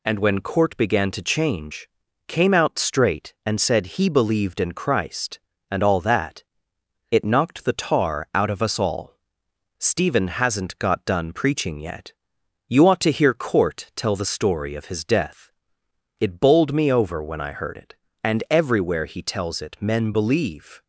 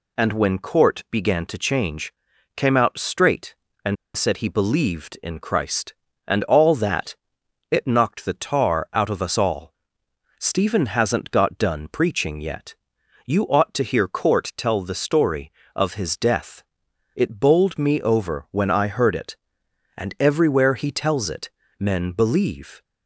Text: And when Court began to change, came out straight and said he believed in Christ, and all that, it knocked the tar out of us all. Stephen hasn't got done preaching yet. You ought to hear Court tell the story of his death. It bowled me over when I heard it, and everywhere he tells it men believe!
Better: first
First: none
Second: pauses between "and" and "said"; slight; at 3.9 s; 0.21 s long // pauses between "it" and "men"; slight; at 21.4 s; 0.28 s long

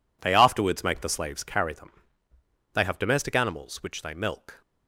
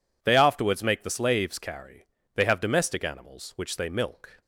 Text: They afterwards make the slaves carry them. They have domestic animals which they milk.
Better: first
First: none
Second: skips "them"; at 2.1 s

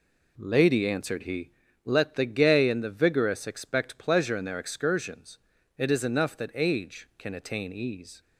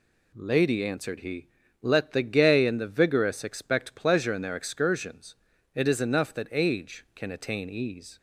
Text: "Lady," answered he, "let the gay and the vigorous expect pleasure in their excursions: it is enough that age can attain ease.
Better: second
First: starts louder than the rest; slight; until 1.7 s; 3 dB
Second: none

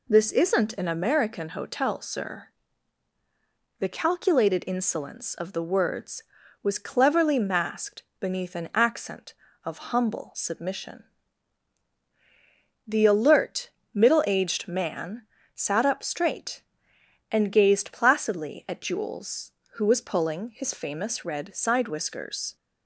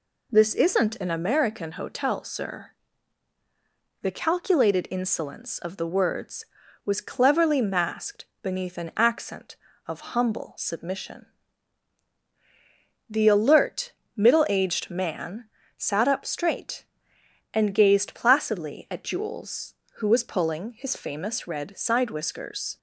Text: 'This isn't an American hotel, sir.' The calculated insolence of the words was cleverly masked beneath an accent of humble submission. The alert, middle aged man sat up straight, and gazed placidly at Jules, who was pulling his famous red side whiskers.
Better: neither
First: pauses between "masked" and "beneath"; slight; at 8.0 s; 0.16 s long // pauses between "man" and "sat"; slight; at 15.2 s; 0.32 s long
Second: pauses between "masked" and "beneath"; slight; at 8.2 s; 0.16 s long // pauses between "man" and "sat"; slight; at 15.4 s; 0.32 s long

